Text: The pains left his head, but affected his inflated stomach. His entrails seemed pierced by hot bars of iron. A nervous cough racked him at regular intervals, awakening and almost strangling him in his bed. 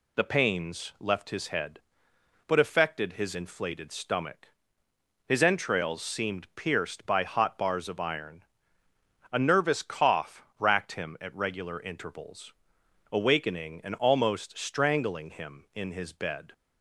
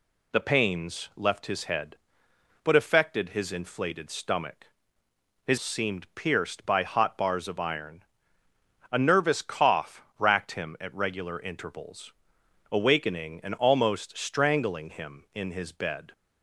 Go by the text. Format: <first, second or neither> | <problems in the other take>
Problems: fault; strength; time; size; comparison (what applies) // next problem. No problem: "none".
first | skips "entrails"; at 5.5 s // pauses between "cough" and "racked"; slight; at 10.0 s; 0.16 s long; slight in the first